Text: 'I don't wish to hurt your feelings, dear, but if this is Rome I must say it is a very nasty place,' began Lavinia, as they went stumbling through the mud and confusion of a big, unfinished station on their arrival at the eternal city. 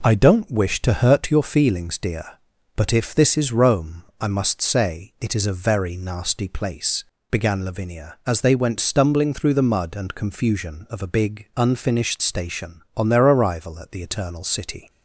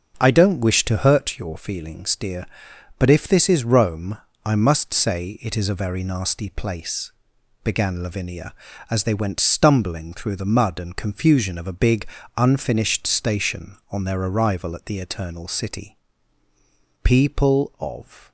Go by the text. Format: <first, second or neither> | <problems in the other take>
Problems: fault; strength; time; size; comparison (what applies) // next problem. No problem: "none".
first | starts louder than the rest; until 1.2 s; 6 dB // pauses between "Rome" and "I"; slight; at 4.1 s; 0.28 s long; slight in the first // goes on to say "People of"; noticeable; from 17.0 s on; 1.2 s long